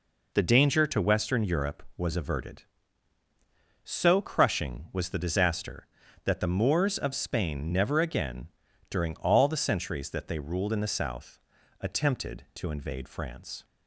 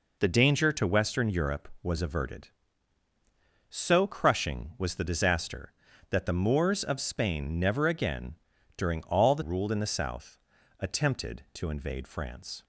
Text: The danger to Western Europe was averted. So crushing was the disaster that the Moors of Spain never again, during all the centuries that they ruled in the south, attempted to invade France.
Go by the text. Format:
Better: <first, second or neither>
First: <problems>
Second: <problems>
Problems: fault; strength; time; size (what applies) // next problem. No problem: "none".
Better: first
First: none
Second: skips "centuries that they"; at 9.4 s